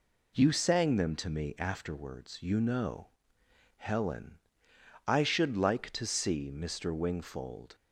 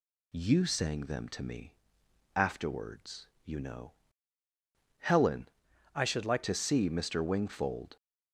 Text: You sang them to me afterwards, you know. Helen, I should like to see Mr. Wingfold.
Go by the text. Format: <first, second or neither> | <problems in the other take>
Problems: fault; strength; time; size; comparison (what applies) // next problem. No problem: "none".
first | pauses between "me" and "afterwards"; noticeable; at 1.7 s; 0.62 s long // changes voice from "I" to "like"; from 5.9 to 6.4 s; 0.5 s long